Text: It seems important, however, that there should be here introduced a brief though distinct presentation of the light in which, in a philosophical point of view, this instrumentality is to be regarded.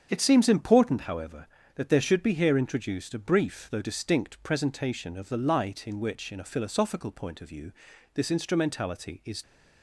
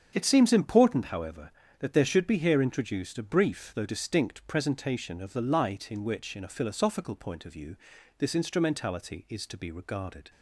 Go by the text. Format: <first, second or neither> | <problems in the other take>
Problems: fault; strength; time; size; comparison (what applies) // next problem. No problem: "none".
second | starts louder than the rest; strong; until 1.1 s; 7.5 dB; strong in the second // stops before "to be regarded"; at 9.4 s